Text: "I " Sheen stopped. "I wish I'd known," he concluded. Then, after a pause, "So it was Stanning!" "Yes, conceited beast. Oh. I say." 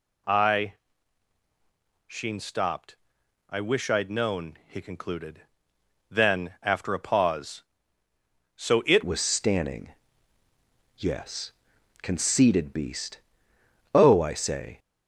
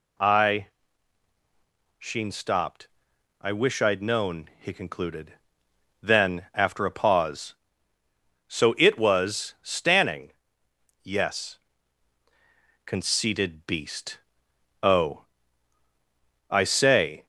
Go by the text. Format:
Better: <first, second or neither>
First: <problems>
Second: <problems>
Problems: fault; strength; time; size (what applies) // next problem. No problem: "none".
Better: second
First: changes voice at "was"; from 9.0 s on; 5.7 s long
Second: none